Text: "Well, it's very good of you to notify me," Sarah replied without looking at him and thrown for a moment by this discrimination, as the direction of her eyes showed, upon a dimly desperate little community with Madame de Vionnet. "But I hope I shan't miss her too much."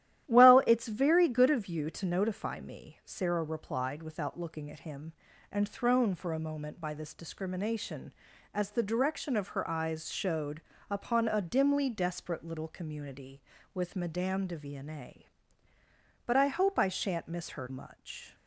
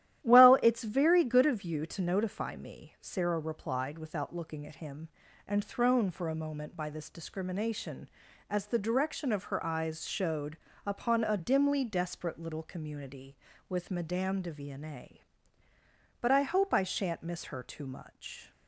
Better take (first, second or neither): second